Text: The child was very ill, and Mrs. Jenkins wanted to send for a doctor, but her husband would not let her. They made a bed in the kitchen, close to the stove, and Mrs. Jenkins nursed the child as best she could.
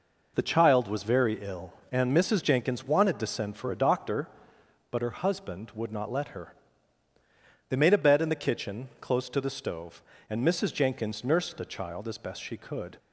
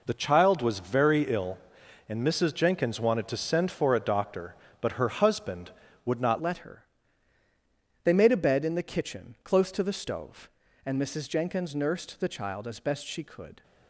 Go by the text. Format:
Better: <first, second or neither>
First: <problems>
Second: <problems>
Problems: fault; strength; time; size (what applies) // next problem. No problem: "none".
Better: first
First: none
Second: changes voice at "let"; from 6.4 s on; 7.2 s long